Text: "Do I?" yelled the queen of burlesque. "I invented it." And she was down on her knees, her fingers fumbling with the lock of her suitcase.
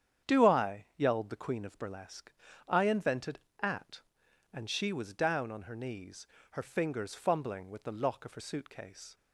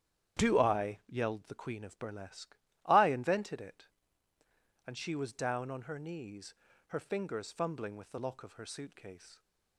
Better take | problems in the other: second | starts louder than the rest; strong; until 1.3 s; 8.5 dB; strong in the second // says "at" for "it"; at 3.5 s

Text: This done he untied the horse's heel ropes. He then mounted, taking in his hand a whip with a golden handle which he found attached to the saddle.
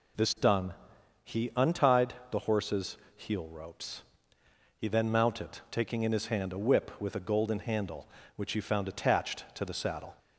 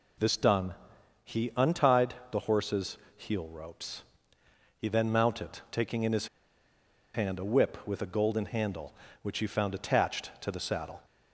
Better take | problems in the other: first | pauses between "done" and "he"; noticeable; at 0.7 s; 0.50 s long; noticeable in the first // pauses between "untied" and "the"; slight; at 2.1 s; 0.16 s long; slight in the first // pauses between "horse's" and "heel"; slight; at 2.9 s; 0.18 s long; slight in the first // pauses between "his" and "hand"; noticeable; at 6.2 s; 0.87 s long

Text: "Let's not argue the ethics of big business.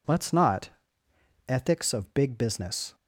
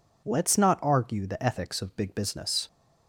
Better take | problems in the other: second | skips "argue the"; at 1.0 s

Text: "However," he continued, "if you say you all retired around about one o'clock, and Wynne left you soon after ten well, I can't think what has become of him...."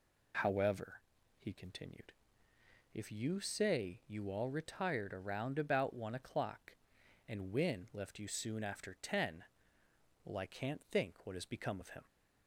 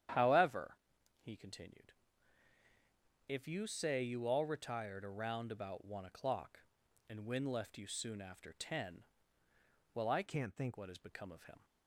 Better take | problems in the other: first | starts louder than the rest; strong; until 1.5 s; 10 dB // pauses between "ten" and "well"; noticeable; at 9.0 s; 0.90 s long; noticeable in the first // changes voice from "can't" to "think"; from 10.2 to 10.7 s; 0.5 s long

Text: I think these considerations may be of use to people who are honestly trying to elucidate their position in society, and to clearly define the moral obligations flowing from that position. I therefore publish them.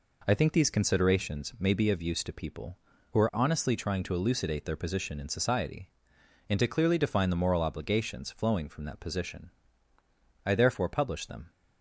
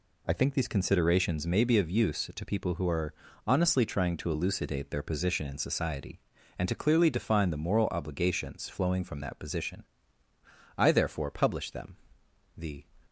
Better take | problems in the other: first | pauses between "are" and "honestly"; slight; at 3.1 s; 0.32 s long // goes on to say "The"; slight; from 12.5 s on; 0.28 s long

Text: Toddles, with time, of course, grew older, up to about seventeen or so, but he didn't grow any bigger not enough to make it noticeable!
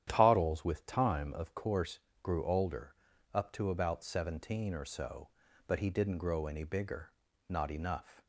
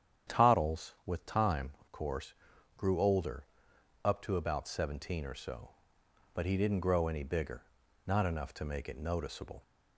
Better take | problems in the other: second | starts louder than the rest; strong; until 1.0 s; 10.5 dB; strong in the second // pauses between "bigger" and "not"; at 7.1 s; 0.38 s long; also in the second // stops before "to make it noticeable"; at 8.2 s

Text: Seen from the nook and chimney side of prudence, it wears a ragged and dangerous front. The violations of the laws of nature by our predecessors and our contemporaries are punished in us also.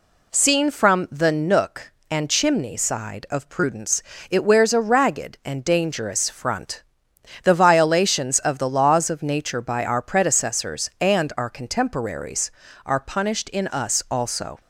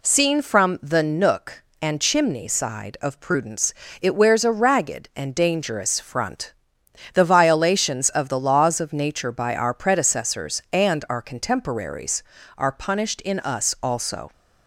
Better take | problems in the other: neither | none

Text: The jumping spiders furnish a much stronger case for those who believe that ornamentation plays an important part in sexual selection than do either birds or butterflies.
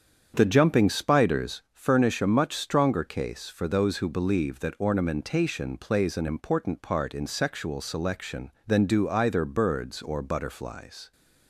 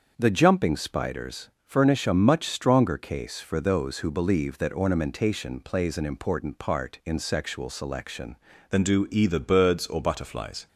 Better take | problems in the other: first | starts louder than the rest; until 1.1 s; 7 dB; strong in the first // pauses between "spiders" and "furnish"; slight; at 1.4 s; 0.16 s long // changes voice at "than"; from 8.7 s on; 1.9 s long

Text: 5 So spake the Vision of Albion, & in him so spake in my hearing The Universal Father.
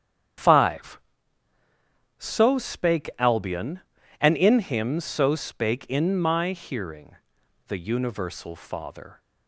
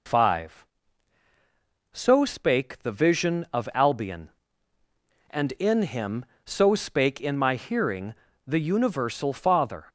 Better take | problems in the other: second | starts louder than the rest; strong; until 2.5 s; 9 dB // skips "the Vision of"; at 3.1 s // pauses between "hearing" and "The"; noticeable; at 7.1 s; 0.50 s long; slight in the second

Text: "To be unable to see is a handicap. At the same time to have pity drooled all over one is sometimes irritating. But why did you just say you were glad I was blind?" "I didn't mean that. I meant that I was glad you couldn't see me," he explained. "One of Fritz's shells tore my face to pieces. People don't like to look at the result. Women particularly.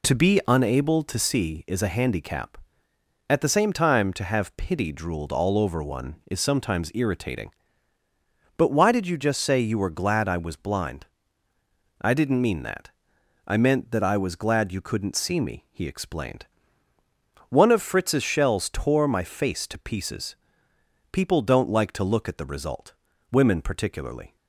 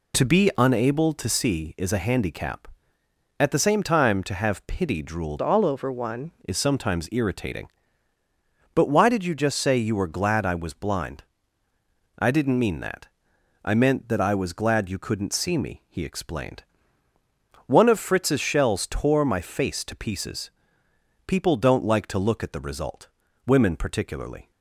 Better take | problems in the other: first | changes voice from "all" to "one"; from 5.4 to 6.3 s; 0.9 s long

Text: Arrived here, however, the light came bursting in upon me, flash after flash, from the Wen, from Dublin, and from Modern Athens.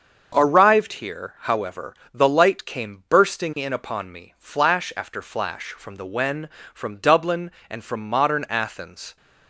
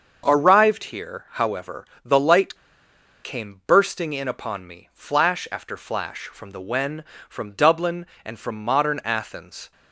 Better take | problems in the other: first | starts louder than the rest; until 1.2 s; 6.5 dB; also in the first // pauses between "light" and "came"; noticeable; at 2.5 s; 0.67 s long

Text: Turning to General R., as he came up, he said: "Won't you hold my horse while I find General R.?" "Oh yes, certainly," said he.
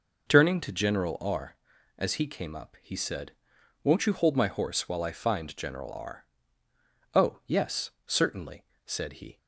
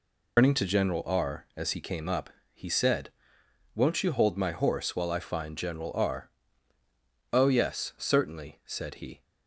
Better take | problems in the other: first | loses the start of "Turning"; at 0.3 s; 130 ms

